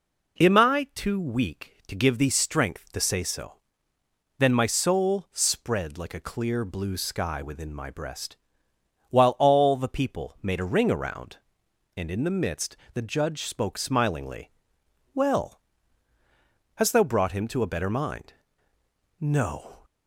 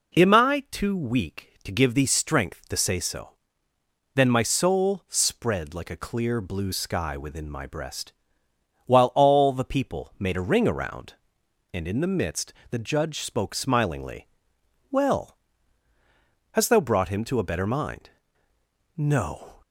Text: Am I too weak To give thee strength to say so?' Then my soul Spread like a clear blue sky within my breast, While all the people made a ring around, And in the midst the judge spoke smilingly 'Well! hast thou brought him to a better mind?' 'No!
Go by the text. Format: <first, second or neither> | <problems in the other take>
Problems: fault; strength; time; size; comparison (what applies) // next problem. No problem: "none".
neither | pauses between "midst" and "the"; slight; the same in both // pauses between "smilingly" and "Well"; noticeable; the same in both